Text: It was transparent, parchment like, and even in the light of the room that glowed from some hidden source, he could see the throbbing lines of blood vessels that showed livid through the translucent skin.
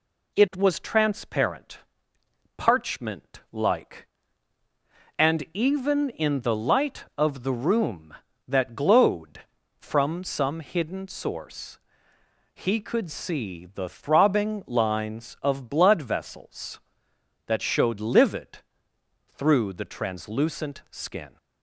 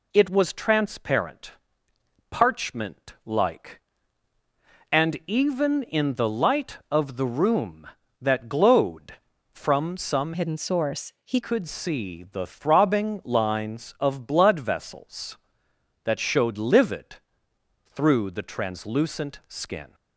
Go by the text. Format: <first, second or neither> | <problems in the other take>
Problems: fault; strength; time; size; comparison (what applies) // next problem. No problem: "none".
first | changes voice from "hidden" to "he"; from 10.3 to 11.3 s; 1.0 s long // pauses between "livid" and "through"; noticeable; at 17.1 s; 0.66 s long; noticeable in the first